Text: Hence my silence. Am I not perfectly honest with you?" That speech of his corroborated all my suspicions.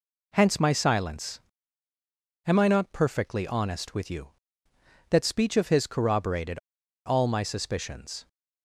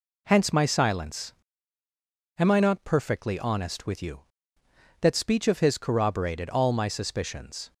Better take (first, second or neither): second